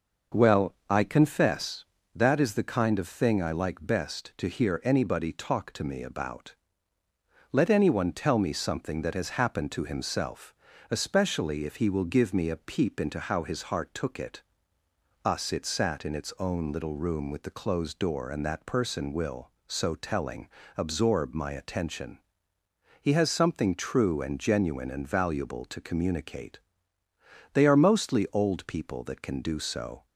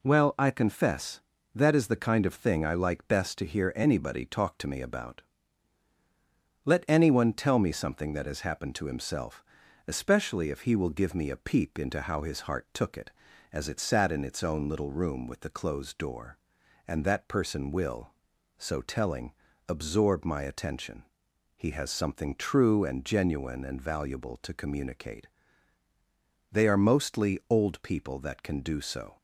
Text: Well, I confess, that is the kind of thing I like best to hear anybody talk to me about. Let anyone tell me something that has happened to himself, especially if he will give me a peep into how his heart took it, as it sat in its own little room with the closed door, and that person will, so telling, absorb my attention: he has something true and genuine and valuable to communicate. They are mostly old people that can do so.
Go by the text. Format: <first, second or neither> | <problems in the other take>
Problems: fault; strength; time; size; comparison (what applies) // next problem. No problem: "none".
second | says "us" for "as"; at 15.2 s